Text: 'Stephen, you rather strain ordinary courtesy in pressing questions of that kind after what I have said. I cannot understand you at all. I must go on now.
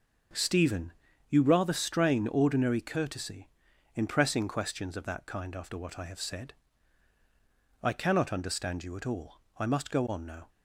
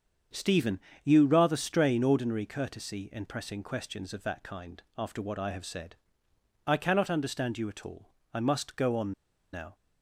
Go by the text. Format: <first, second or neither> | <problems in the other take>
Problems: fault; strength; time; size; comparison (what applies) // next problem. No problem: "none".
first | starts louder than the rest; strong; until 1.5 s; 7 dB // pauses between "on" and "now"; at 9.1 s; 0.41 s long